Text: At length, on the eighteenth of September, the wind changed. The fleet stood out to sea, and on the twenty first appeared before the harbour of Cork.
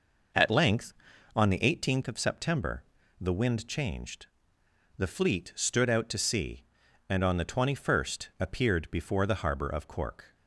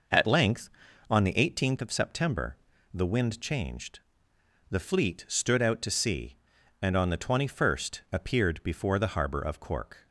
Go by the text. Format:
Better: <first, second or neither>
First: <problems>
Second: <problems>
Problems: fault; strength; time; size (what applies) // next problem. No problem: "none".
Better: neither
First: none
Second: none